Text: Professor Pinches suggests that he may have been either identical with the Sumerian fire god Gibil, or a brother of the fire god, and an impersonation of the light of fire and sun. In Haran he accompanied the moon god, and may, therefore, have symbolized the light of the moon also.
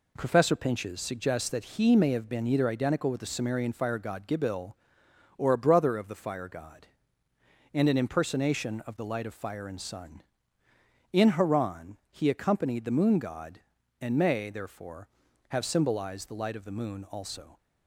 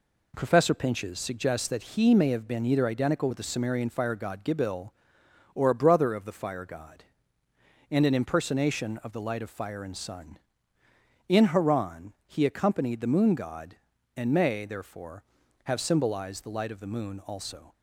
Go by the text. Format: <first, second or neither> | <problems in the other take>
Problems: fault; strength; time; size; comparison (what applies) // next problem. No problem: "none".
neither | none